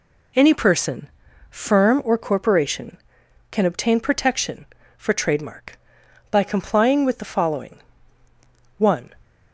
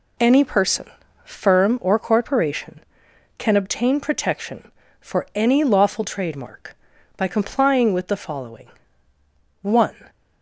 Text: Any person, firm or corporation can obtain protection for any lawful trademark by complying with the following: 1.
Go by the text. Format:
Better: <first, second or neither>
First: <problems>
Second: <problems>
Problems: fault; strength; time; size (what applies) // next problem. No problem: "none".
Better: second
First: skips "any lawful"; at 5.1 s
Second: none